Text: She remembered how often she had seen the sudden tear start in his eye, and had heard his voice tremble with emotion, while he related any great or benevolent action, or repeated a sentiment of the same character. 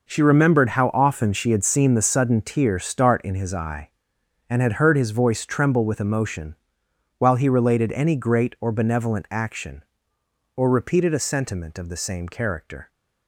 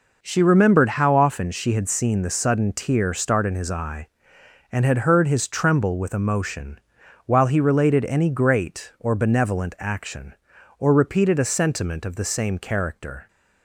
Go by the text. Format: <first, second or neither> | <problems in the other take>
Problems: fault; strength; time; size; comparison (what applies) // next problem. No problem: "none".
first | skips "voice"; at 5.4 s